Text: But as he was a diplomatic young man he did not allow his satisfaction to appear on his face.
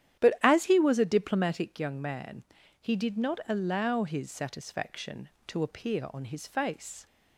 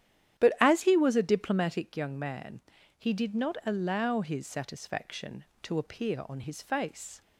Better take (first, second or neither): neither